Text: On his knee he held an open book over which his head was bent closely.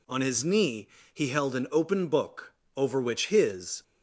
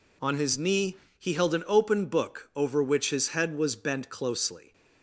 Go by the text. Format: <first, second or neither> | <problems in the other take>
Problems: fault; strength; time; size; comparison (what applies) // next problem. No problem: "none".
second | pauses between "knee" and "he"; slight; at 0.8 s; 0.28 s long; slight in the second // pauses between "book" and "over"; slight; at 2.5 s; 0.24 s long // stops before "head was bent closely"; at 3.8 s